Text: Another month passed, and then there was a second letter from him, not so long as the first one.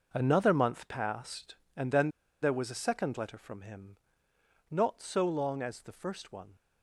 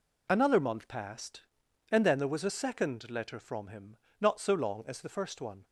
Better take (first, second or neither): second